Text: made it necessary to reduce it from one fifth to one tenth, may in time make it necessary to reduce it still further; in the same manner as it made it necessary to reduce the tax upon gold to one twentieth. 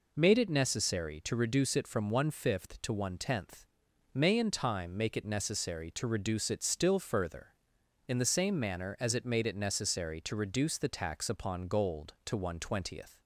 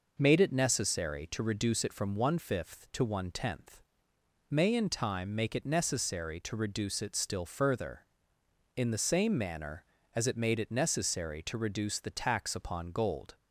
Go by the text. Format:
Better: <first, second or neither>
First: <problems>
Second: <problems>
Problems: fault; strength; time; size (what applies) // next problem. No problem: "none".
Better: first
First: none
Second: stops before "to one twentieth"; at 13.3 s